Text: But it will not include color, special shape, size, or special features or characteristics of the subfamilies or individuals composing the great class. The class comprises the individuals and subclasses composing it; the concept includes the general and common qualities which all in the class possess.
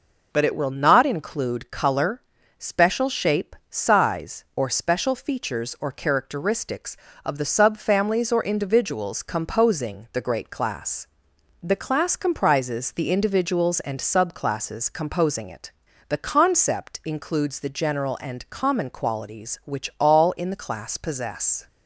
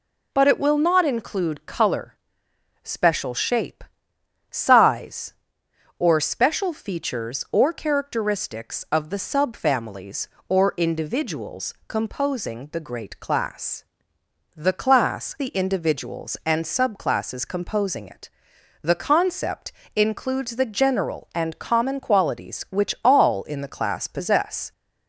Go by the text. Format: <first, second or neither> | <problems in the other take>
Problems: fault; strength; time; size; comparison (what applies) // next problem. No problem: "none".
first | skips "comprises"; at 15.3 s // pauses between "concept" and "includes"; slight; at 19.7 s; 0.24 s long